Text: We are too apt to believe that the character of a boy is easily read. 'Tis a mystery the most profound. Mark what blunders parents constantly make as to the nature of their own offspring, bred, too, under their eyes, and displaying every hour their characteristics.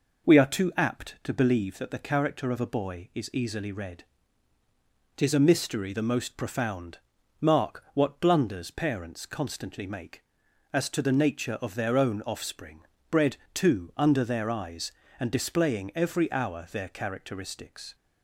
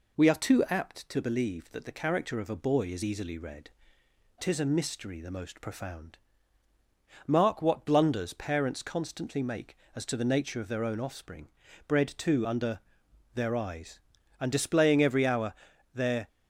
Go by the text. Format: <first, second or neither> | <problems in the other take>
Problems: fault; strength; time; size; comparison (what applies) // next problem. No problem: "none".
first | pauses between "under" and "their"; noticeable; at 12.7 s; 0.56 s long // pauses between "hour" and "their"; at 15.5 s; 0.40 s long // stops before "characteristics"; at 16.2 s